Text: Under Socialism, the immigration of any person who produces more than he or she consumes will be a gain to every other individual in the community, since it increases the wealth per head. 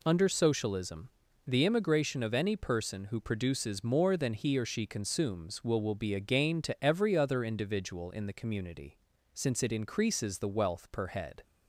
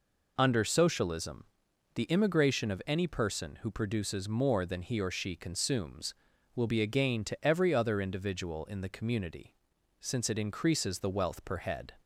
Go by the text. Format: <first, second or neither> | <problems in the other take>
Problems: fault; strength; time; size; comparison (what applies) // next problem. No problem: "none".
second | says "will" twice; at 5.7 s